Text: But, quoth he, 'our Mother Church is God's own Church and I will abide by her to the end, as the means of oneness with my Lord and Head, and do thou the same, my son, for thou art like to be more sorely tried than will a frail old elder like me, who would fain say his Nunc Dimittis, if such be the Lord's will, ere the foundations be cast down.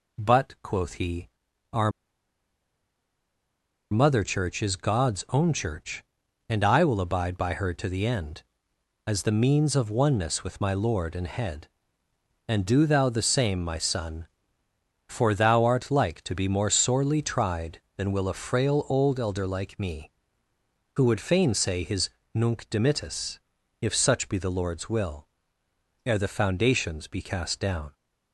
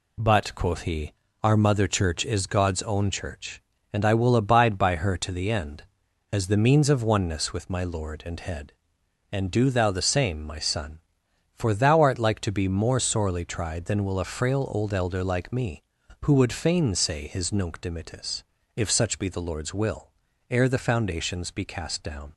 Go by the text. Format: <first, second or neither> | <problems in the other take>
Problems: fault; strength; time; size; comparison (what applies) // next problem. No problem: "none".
second | pauses between "our" and "Mother"; strong; at 1.8 s; 2.0 s long // pauses between "his" and "Nunc"; slight; at 22.0 s; 0.24 s long